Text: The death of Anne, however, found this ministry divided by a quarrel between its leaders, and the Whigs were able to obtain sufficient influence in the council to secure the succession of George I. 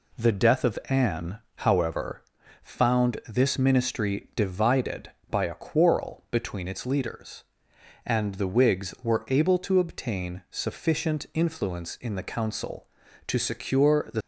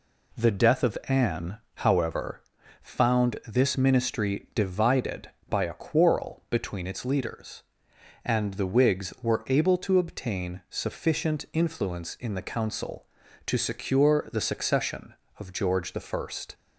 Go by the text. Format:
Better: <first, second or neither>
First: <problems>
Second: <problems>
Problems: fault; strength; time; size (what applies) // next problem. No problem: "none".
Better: second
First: stops before "succession of George I"; at 14.2 s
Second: none